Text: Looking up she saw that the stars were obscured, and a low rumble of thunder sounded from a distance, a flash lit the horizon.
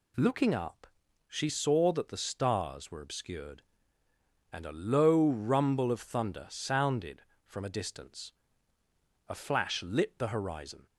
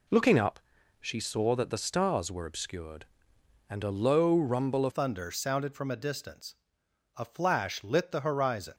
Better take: first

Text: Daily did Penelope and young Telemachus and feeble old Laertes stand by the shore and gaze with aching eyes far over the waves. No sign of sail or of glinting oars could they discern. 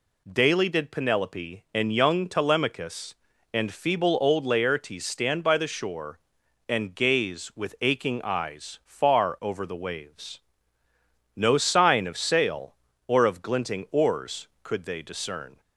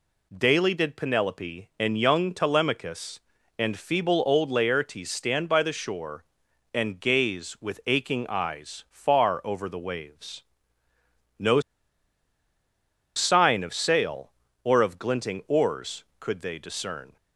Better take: first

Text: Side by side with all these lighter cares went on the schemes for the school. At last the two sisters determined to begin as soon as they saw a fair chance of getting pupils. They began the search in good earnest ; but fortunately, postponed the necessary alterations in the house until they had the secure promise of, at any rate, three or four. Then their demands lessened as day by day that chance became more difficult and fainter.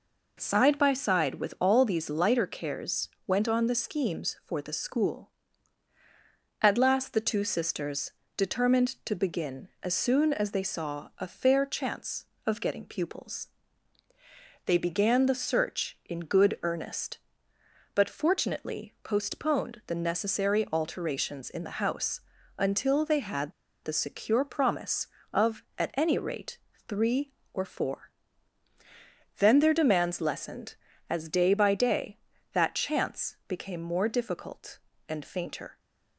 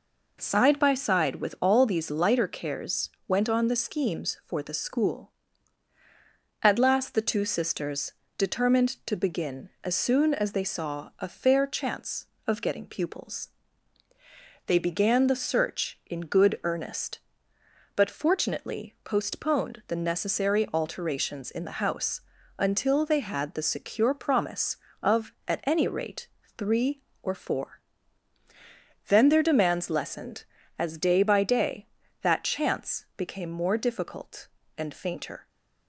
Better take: second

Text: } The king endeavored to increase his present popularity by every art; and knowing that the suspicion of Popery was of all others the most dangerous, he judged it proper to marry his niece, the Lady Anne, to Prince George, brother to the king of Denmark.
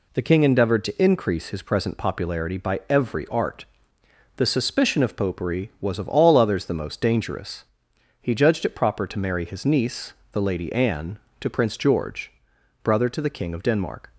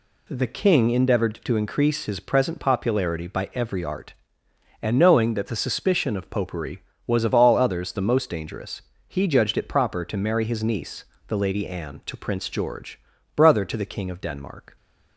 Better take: second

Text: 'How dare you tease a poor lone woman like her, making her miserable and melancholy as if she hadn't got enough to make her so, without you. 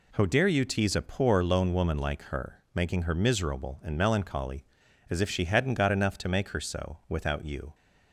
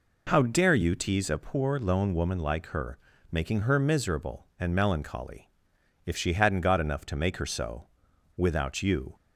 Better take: first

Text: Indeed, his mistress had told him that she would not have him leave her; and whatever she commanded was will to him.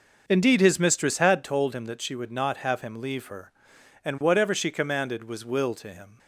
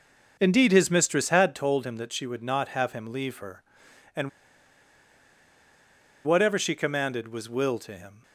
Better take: first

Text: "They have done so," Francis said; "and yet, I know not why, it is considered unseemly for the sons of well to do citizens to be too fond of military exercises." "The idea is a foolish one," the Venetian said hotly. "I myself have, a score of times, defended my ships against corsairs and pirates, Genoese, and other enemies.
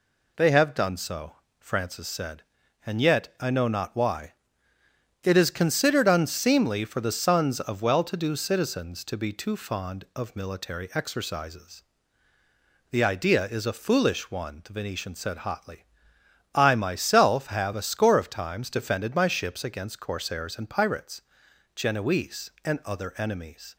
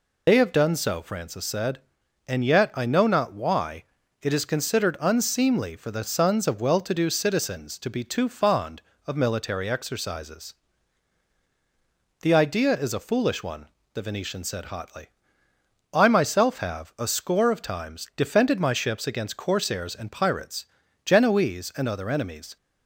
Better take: first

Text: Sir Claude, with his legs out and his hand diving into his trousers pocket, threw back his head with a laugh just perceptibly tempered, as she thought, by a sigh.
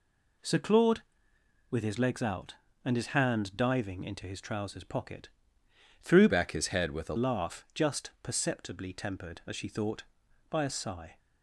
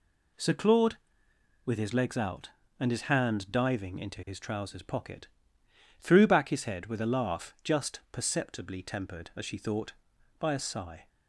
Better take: second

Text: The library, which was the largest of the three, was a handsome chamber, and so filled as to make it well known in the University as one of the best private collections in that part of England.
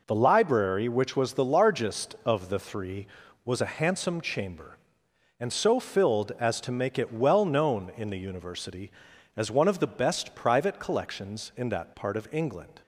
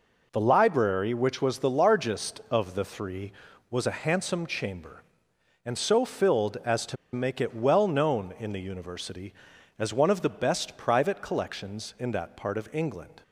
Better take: first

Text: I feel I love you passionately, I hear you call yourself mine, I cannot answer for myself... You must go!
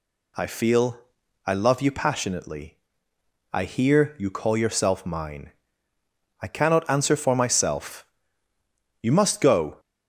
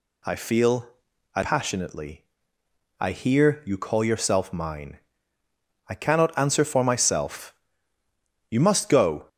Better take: first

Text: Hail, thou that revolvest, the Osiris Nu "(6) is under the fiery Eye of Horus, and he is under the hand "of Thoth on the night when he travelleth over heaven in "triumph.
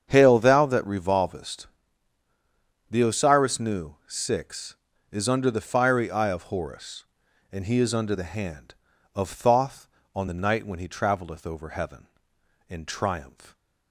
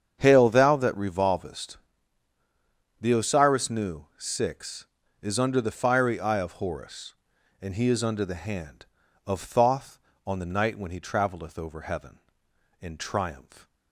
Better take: neither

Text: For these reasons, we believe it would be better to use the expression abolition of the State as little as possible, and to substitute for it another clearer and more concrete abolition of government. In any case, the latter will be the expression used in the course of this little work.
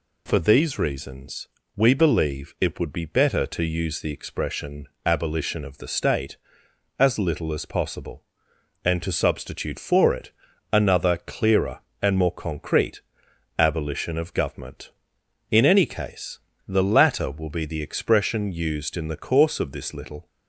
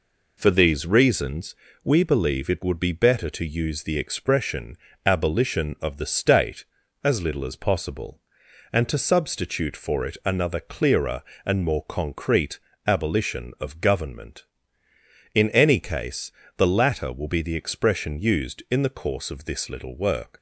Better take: second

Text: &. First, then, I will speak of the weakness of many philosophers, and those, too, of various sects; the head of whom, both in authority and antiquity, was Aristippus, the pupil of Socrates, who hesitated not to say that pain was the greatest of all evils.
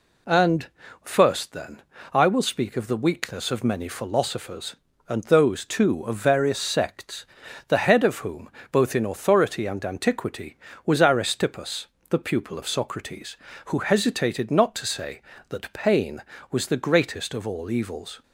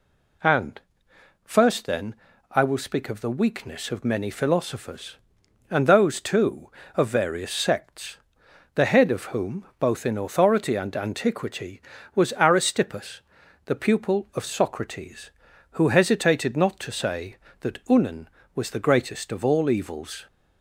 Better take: first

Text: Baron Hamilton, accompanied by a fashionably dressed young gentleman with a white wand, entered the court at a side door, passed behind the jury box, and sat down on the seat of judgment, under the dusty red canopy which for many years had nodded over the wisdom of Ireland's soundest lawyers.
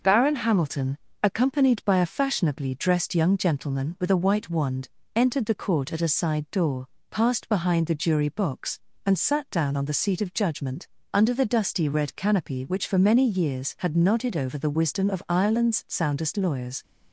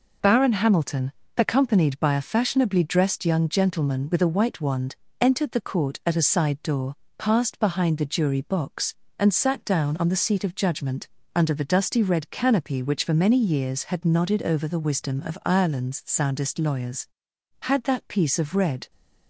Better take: first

